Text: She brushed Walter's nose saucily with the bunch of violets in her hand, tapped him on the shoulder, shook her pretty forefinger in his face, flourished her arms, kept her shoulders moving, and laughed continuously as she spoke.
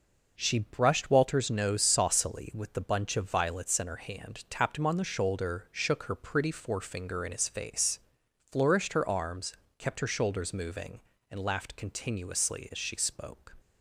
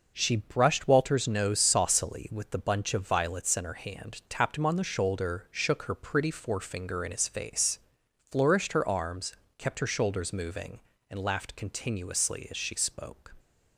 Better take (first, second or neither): neither